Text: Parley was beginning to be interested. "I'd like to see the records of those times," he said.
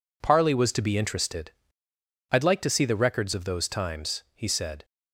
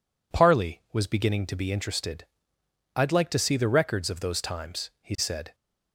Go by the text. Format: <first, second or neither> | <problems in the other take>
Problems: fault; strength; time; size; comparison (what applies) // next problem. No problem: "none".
second | skips "beginning"; at 0.7 s